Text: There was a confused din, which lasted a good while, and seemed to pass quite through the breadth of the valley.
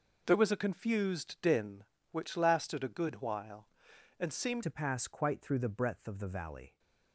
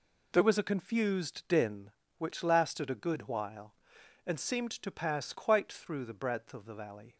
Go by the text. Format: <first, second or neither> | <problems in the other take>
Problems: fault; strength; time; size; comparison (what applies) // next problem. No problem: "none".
second | changes voice at "to"; from 4.6 s on; 2.1 s long